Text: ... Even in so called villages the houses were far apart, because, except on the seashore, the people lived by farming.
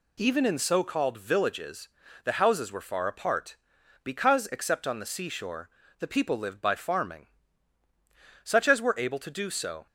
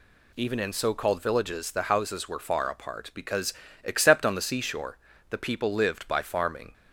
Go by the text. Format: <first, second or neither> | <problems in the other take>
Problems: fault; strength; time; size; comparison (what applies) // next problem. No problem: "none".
second | pauses between "villages" and "the"; slight; at 1.8 s; 0.34 s long // goes on to say "Such as were able to do so"; from 8.4 s on; 1.4 s long